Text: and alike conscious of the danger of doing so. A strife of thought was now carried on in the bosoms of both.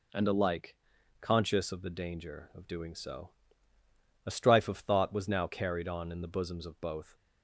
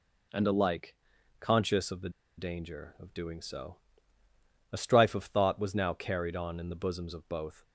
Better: first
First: pauses between "alike" and "conscious"; noticeable; at 0.7 s; 0.46 s long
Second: pauses between "alike" and "conscious"; noticeable; at 0.9 s; 0.46 s long // pauses between "the" and "danger"; slight; at 2.0 s; 0.27 s long

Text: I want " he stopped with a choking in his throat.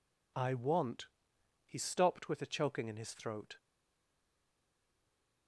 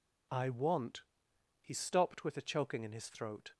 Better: second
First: stays silent after the last word; noticeable; from 3.5 s on; 1.9 s long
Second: none

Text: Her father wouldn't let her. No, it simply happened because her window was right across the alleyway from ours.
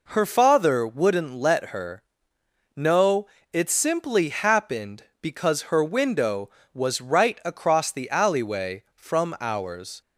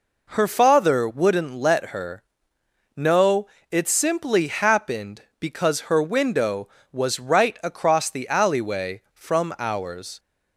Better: neither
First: none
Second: none

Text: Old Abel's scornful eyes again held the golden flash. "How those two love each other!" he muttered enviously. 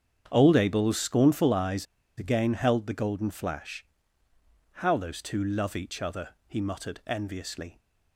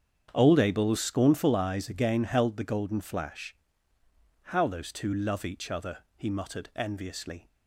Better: second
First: starts louder than the rest; strong; until 1.3 s; 8 dB // pauses between "eyes" and "again"; slight; at 1.8 s; 0.32 s long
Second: starts louder than the rest; strong; until 1.3 s; 8 dB

